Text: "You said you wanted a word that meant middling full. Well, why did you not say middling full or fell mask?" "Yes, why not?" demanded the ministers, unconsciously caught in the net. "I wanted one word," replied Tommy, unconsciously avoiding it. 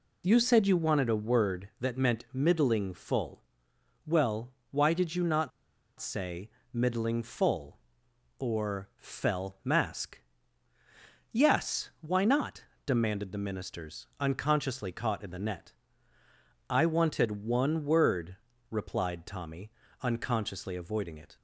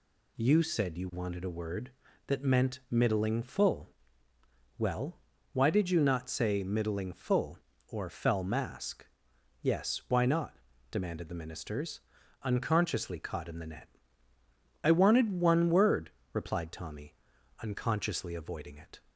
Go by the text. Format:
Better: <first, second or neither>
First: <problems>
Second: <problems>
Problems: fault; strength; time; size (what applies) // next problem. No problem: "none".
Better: second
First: pauses between "not" and "say"; noticeable; at 5.5 s; 0.49 s long // pauses between "say" and "middling"; slight; at 6.4 s; 0.24 s long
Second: none